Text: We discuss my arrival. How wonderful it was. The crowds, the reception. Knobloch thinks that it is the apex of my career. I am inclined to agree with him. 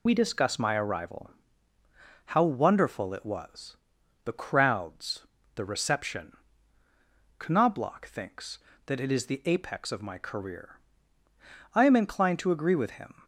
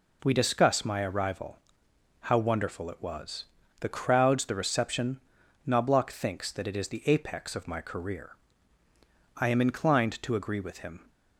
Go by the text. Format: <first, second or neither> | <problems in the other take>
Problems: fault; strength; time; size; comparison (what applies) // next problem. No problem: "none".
second | loses the start of "We"; at 0.0 s; 50 ms